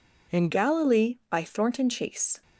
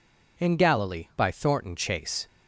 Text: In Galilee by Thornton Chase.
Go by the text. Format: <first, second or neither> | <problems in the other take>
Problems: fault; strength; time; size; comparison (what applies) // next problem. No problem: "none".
second | changes voice at "Galilee"; from 0.5 s on; 1.9 s long